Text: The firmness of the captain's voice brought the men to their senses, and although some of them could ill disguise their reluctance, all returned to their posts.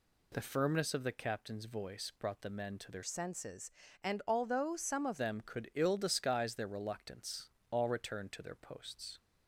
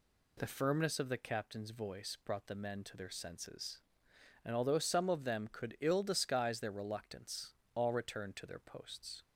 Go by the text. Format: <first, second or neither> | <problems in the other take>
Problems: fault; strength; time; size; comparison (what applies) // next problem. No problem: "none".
second | changes voice from "senses" to "of"; from 3.0 to 5.2 s; 2.2 s long